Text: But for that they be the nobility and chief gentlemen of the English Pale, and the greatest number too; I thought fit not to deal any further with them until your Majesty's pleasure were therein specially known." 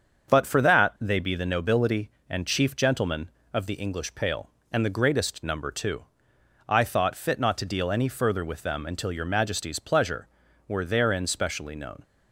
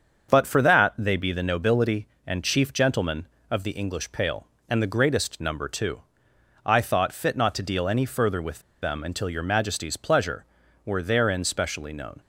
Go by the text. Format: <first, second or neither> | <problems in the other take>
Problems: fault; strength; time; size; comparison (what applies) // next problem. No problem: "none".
first | starts louder than the rest; until 1.3 s; 7 dB; also in the first // pauses between "with" and "them"; slight; at 8.5 s; 0.22 s long